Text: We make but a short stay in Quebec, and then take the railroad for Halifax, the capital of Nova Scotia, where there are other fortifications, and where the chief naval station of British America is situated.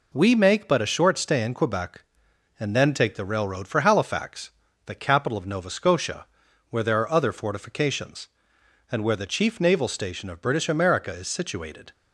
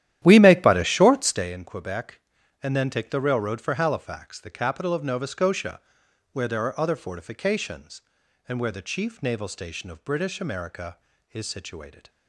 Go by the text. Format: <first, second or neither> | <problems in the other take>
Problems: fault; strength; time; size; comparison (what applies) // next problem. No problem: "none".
first | starts louder than the rest; strong; until 1.5 s; 12 dB